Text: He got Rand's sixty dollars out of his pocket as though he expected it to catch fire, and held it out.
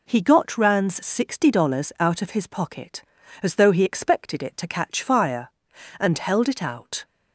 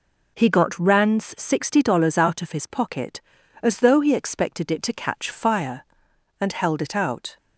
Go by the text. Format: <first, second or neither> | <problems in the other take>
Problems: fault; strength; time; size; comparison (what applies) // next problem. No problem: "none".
neither | none